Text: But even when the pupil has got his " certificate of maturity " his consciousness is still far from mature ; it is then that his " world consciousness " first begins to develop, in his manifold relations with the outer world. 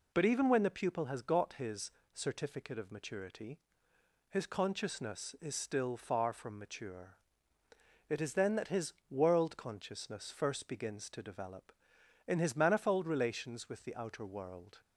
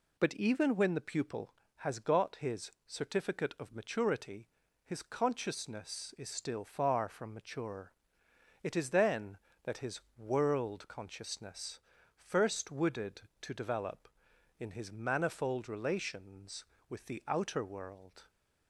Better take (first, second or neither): first